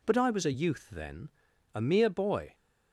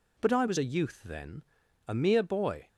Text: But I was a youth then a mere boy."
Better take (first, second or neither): neither